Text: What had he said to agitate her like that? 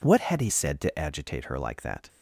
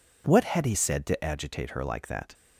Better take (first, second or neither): neither